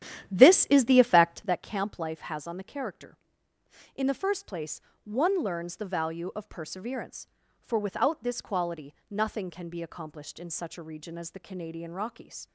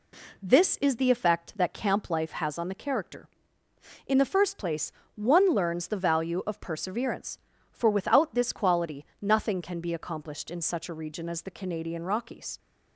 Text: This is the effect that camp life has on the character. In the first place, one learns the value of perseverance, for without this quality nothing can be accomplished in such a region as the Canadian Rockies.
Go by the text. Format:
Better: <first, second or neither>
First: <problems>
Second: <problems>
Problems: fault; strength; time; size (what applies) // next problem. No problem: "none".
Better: second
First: starts louder than the rest; strong; until 1.6 s; 11 dB // pauses between "quality" and "nothing"; slight; at 8.9 s; 0.16 s long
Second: pauses between "quality" and "nothing"; slight; at 9.0 s; 0.16 s long